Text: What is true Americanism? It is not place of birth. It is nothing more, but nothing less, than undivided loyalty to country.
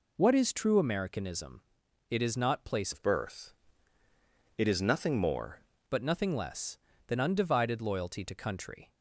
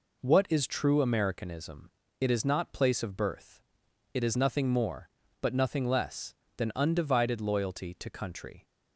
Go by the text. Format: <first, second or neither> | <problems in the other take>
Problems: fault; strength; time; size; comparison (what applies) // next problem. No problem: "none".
second | changes voice from "of" to "more"; from 2.9 to 5.6 s; 2.7 s long